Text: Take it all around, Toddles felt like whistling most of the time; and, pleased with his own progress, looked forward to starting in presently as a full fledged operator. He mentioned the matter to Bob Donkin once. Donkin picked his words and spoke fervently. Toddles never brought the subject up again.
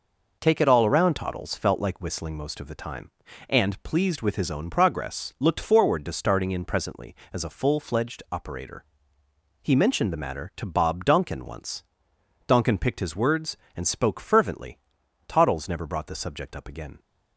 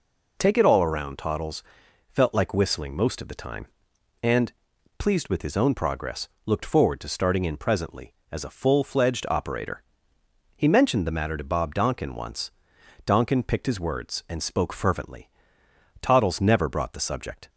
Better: first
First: none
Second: pauses between "Toddles" and "felt"; noticeable; at 1.6 s; 0.48 s long // stops before "up again"; at 17.4 s

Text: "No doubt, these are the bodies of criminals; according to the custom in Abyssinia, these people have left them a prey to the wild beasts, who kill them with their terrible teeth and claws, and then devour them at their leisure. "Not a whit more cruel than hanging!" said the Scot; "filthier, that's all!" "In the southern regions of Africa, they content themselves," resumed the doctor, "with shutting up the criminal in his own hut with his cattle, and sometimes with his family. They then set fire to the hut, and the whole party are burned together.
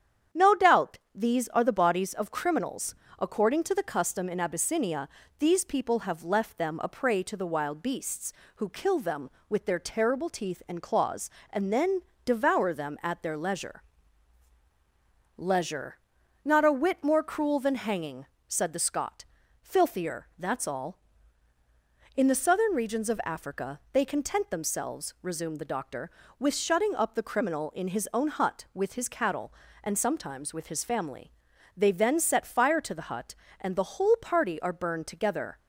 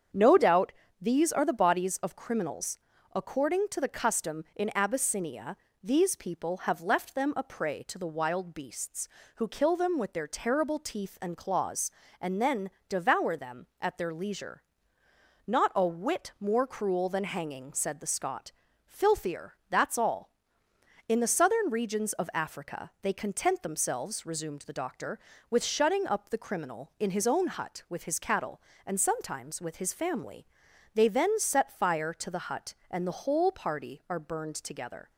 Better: second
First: starts louder than the rest; strong; until 1.5 s; 9 dB // pauses between "then" and "devour"; slight; at 12.0 s; 0.22 s long // says "leisure" twice; at 15.3 s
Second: starts louder than the rest; strong; until 1.4 s; 7.5 dB // pauses between "then" and "devour"; slight; at 12.6 s; 0.18 s long

